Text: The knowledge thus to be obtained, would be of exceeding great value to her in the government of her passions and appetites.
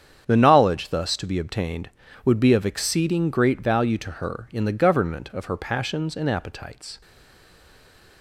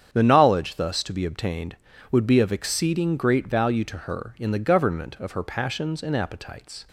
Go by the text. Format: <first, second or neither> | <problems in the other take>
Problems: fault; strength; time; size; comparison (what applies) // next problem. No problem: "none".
second | starts louder than the rest; strong; until 1.2 s; 8 dB; strong in the second // stays silent after the last word; noticeable; from 7.0 s on; 1.2 s long